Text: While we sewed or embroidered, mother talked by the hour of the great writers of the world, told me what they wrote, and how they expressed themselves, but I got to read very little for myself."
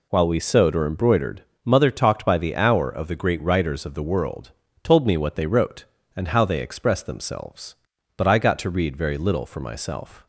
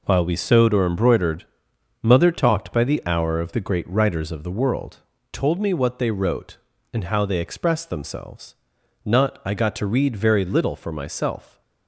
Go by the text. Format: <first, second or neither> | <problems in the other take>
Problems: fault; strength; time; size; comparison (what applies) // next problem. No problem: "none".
first | says "not" for "but"; at 9.0 s